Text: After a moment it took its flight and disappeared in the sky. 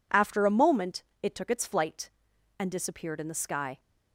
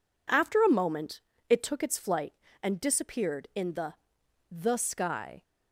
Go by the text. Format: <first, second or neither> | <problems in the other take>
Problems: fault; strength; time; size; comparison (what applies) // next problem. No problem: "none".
first | pauses between "moment" and "it"; slight; at 1.2 s; 0.28 s long; slight in the first // says "the" twice; at 4.5 s